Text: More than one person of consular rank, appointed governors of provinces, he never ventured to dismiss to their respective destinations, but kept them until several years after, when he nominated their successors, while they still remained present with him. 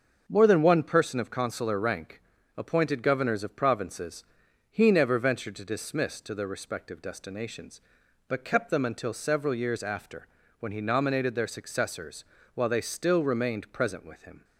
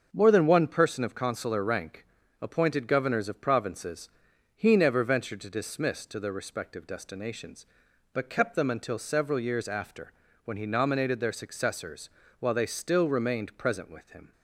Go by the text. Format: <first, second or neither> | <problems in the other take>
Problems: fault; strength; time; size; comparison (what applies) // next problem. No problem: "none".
neither | starts louder than the rest; the same in both